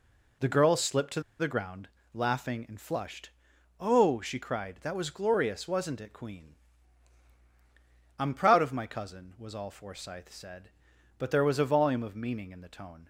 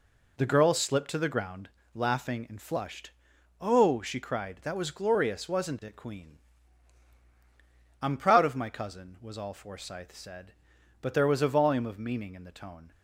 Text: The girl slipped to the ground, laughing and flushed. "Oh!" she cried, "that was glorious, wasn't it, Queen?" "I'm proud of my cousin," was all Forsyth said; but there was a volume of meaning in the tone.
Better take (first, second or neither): second